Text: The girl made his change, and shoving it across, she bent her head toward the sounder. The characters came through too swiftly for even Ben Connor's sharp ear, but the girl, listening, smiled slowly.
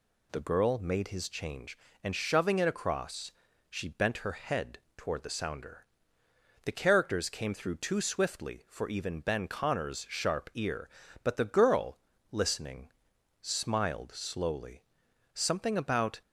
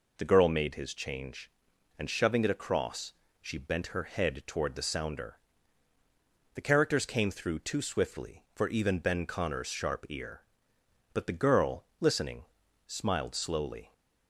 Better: second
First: pauses between "head" and "toward"; slight; at 4.7 s; 0.18 s long // goes on to say "Something about"; noticeable; from 15.3 s on; 0.88 s long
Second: none

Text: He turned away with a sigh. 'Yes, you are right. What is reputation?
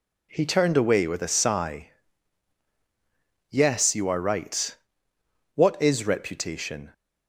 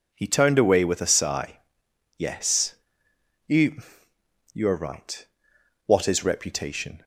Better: first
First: none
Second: says "you" twice; at 4.5 s

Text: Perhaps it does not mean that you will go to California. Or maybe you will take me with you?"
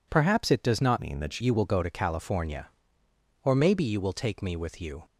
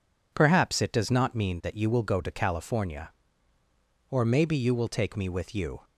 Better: second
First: changes voice from "mean" to "that"; from 1.0 to 1.4 s; 0.4 s long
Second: none

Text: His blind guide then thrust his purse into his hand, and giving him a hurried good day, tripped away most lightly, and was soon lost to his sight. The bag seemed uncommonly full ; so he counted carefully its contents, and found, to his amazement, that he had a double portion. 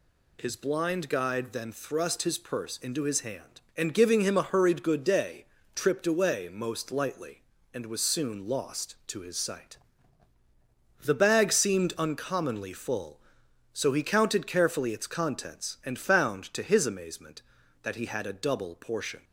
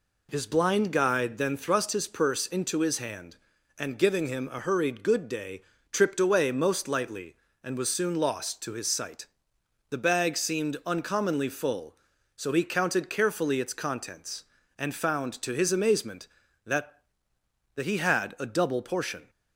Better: first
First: none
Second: says "that" twice; at 17.7 s

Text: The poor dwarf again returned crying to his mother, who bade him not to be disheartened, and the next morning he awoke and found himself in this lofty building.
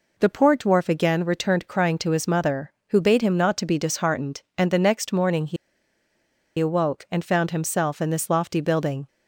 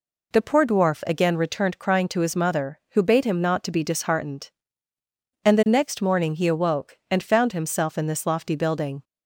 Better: second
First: pauses between "he" and "awoke"; at 5.5 s; 1.0 s long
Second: none

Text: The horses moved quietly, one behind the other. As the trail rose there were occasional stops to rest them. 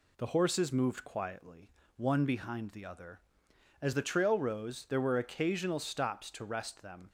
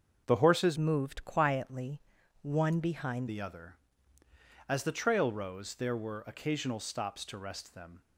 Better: first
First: none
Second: starts louder than the rest; until 1.2 s; 6.5 dB // changes voice from "moved" to "behind"; from 0.7 to 3.2 s; 2.5 s long

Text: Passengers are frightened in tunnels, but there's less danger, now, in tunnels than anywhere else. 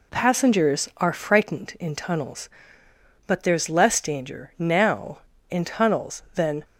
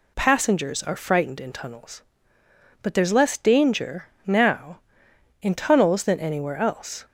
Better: second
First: stops before "anywhere else"; at 6.6 s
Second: none

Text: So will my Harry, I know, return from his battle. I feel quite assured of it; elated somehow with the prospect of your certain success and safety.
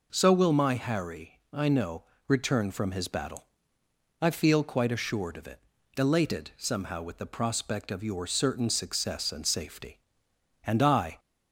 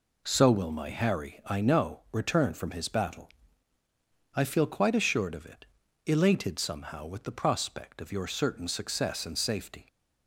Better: second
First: goes on to say "And I"; from 10.6 s on; 0.54 s long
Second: none

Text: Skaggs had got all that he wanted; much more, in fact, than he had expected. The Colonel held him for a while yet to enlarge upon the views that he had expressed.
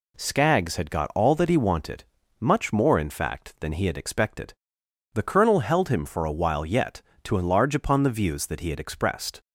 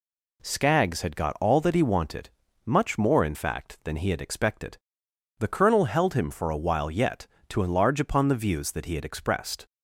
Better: neither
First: none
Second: none

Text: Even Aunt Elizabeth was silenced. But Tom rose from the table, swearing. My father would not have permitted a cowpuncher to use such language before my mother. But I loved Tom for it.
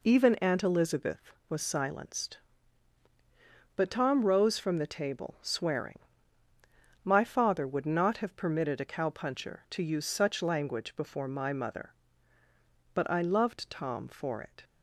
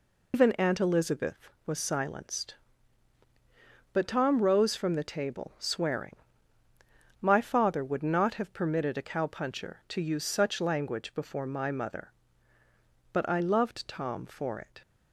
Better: first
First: none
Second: loses the start of "Even"; at 0.3 s; 140 ms

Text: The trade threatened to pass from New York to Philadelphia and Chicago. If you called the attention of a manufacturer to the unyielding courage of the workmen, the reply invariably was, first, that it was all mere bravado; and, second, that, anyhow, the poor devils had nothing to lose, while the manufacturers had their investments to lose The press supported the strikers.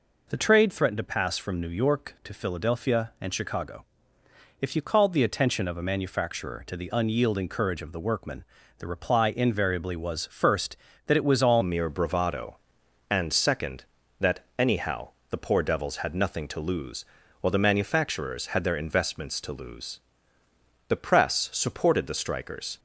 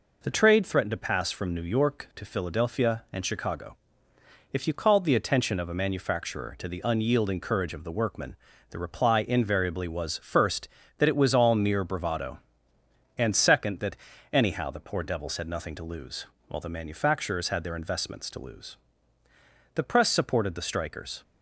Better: second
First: changes voice at "mere"; from 11.6 s on; 11.1 s long // pauses between "lose" and "The"; noticeable; at 19.9 s; 0.88 s long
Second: pauses between "lose" and "The"; noticeable; at 18.7 s; 0.98 s long

